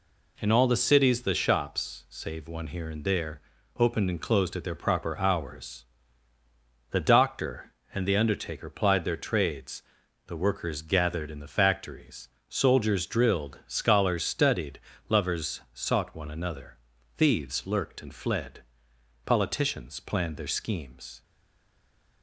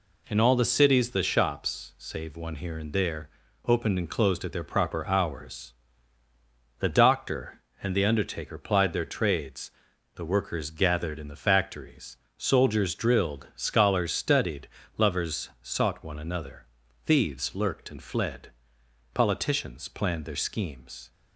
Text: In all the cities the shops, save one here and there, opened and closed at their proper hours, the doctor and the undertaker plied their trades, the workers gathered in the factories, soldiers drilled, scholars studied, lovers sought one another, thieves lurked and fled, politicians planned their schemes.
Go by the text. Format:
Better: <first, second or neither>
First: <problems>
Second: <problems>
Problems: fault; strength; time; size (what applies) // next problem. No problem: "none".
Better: second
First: stays silent after the last word; from 21.2 s on; 1.0 s long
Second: none